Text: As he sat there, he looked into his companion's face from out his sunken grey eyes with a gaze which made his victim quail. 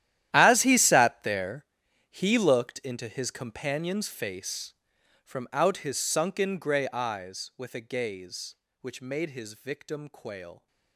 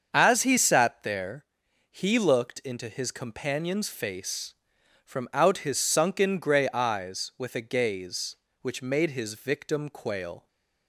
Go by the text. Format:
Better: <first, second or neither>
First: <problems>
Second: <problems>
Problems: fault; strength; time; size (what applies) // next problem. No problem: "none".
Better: second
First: gets quieter; strong; throughout; 17.5 dB // starts louder than the rest; strong; until 1.3 s; 12 dB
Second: starts louder than the rest; until 1.1 s; 7 dB